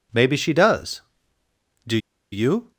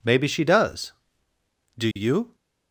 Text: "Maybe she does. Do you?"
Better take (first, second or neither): second